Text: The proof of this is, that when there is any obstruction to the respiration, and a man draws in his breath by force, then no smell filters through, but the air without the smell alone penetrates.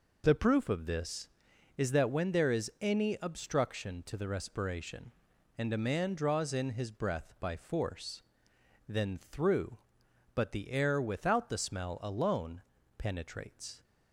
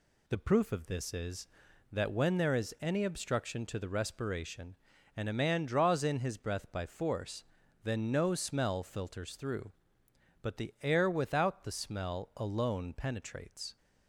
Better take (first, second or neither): second